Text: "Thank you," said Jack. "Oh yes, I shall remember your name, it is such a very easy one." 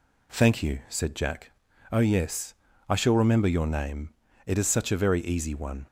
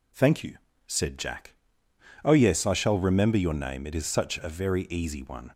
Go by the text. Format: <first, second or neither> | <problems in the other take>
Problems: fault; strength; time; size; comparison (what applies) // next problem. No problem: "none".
neither | none